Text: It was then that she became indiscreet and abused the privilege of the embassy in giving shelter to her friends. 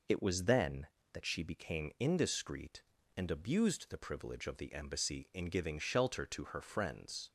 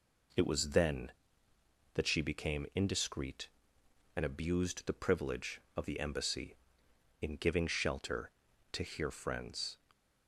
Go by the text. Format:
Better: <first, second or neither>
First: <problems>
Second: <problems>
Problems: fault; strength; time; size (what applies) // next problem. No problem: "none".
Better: first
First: none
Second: says "here" for "her"; at 8.8 s